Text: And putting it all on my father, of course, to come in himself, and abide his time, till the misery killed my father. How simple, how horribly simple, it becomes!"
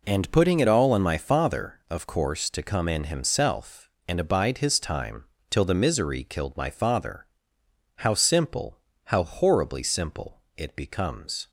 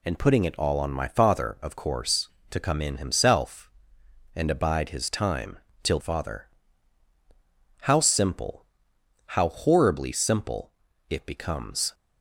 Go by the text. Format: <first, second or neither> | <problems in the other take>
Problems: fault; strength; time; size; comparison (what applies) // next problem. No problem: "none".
first | skips "the misery killed my"; at 5.9 s